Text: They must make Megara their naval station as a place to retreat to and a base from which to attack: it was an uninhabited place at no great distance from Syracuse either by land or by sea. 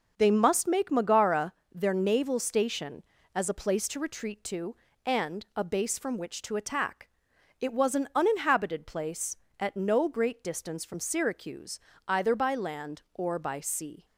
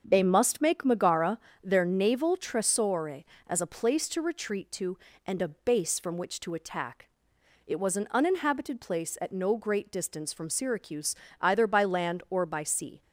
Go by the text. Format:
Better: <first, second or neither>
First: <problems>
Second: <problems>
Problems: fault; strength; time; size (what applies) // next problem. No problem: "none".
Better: first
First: pauses between "Megara" and "their"; slight; at 1.5 s; 0.20 s long // pauses between "Syracuse" and "either"; slight; at 11.8 s; 0.26 s long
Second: starts louder than the rest; until 1.0 s; 7 dB // pauses between "Megara" and "their"; slight; at 1.3 s; 0.24 s long // says "tresore" for "station"; at 2.3 s // pauses between "Syracuse" and "either"; slight; at 11.1 s; 0.26 s long